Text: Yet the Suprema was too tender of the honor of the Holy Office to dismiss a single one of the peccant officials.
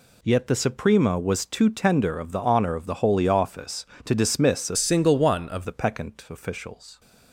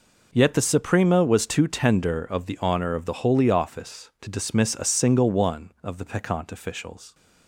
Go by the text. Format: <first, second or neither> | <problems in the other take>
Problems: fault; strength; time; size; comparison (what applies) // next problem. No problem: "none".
second | changes voice from "single" to "of"; from 4.7 to 5.6 s; 0.9 s long